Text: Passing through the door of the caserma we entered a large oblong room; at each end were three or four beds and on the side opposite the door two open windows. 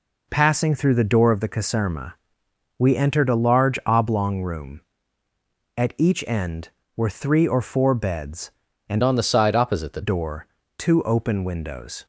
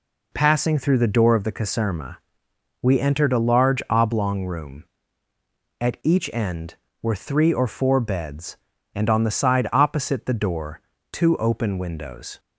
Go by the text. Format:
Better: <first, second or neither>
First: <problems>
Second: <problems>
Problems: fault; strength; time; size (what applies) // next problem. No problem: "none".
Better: second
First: pauses between "caserma" and "we"; noticeable; at 2.1 s; 0.62 s long // changes voice from "on" to "the"; from 9.0 to 10.0 s; 1.0 s long // pauses between "door" and "two"; slight; at 10.4 s; 0.30 s long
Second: pauses between "caserma" and "we"; noticeable; at 2.1 s; 0.62 s long // pauses between "door" and "two"; slight; at 10.8 s; 0.30 s long